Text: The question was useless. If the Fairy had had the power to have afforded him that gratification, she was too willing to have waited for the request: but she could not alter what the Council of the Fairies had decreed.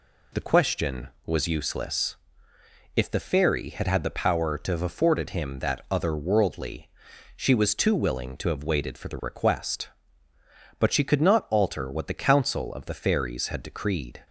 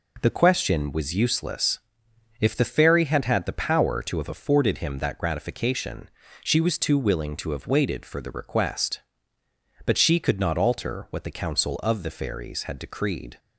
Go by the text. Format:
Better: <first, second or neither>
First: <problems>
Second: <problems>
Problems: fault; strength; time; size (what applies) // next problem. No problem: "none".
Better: second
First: says "otherworldly" for "gratification"; at 5.8 s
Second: none